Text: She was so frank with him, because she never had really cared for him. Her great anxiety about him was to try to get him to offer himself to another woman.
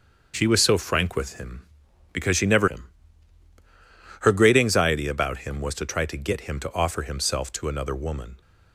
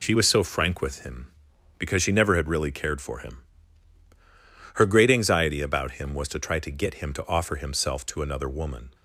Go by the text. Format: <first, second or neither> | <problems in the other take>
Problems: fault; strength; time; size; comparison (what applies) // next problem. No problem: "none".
second | starts louder than the rest; until 1.3 s; 6.5 dB // skips "had really cared for"; at 2.6 s